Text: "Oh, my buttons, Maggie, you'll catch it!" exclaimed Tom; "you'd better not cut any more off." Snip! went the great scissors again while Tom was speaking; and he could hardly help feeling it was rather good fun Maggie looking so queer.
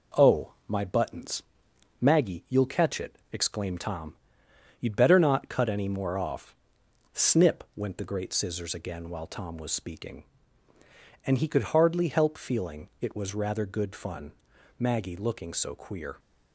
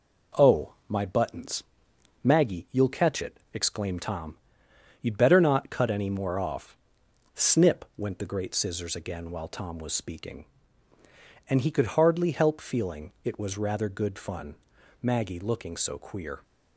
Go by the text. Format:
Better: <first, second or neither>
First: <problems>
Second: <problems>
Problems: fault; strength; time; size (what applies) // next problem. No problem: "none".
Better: neither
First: pauses between "fun" and "Maggie"; noticeable; at 14.3 s; 0.48 s long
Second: pauses between "fun" and "Maggie"; noticeable; at 14.5 s; 0.48 s long